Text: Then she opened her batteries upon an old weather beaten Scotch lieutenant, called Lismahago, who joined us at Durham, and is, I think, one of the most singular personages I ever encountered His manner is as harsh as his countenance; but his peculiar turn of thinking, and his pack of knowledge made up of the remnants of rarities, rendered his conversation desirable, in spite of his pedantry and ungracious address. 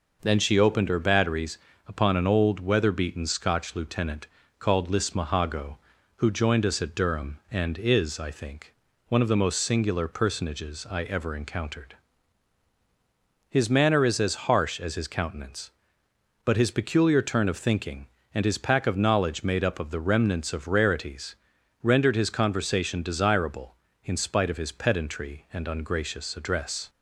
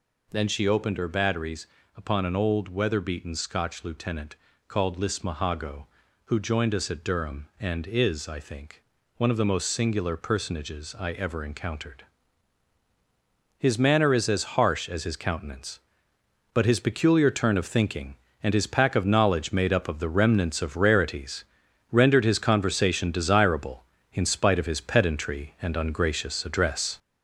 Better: first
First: pauses between "batteries" and "upon"; slight; at 1.5 s; 0.30 s long // pauses between "encountered" and "His"; strong; at 11.9 s; 1.5 s long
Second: gets louder; noticeable; throughout; 5 dB // pauses between "batteries" and "upon"; slight; at 1.6 s; 0.30 s long // pauses between "encountered" and "His"; strong; at 12.0 s; 1.5 s long

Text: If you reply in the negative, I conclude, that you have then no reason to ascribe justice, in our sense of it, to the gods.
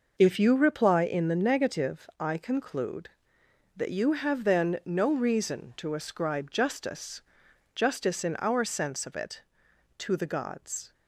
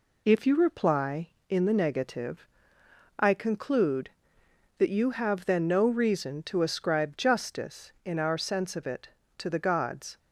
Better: second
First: says "justice" twice; at 7.7 s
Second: none

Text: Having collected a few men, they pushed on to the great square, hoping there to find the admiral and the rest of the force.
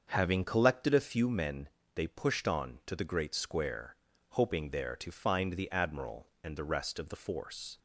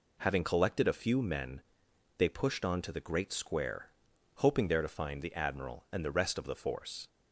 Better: second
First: starts louder than the rest; until 1.2 s; 6.5 dB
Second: none

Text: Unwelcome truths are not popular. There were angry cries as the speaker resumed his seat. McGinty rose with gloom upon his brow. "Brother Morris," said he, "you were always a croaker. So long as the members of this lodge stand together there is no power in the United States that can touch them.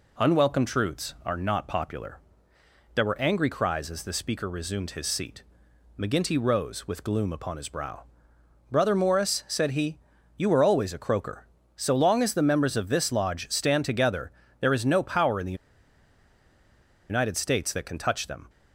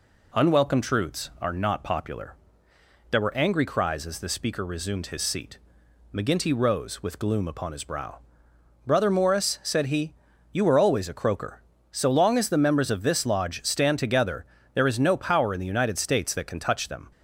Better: second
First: pauses between "together" and "there"; slight; at 14.3 s; 0.28 s long // pauses between "the" and "United"; strong; at 15.5 s; 1.5 s long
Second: pauses between "together" and "there"; slight; at 14.4 s; 0.28 s long

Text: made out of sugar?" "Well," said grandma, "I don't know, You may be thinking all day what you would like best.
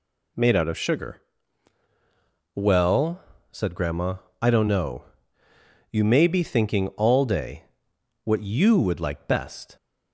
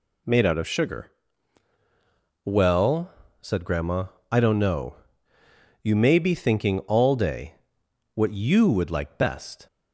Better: neither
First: pauses between "day" and "what"; noticeable; at 7.6 s; 0.60 s long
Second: pauses between "day" and "what"; noticeable; at 7.5 s; 0.60 s long

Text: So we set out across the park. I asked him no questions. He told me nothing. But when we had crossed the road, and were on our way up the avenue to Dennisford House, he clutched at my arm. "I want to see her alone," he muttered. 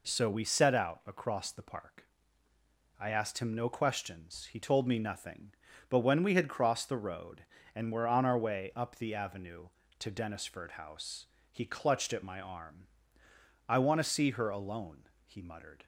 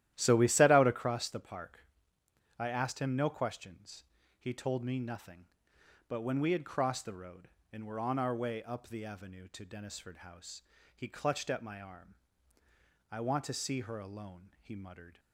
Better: first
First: none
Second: starts louder than the rest; strong; until 1.1 s; 12.5 dB

